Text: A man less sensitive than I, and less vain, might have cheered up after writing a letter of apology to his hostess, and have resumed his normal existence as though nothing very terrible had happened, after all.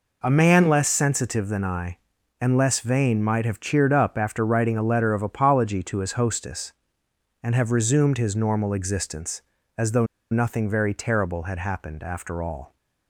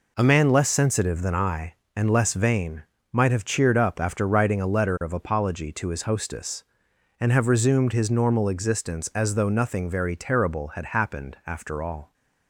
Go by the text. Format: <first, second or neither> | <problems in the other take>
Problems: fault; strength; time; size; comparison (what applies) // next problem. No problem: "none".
second | pauses between "though" and "nothing"; slight; at 10.0 s; 0.25 s long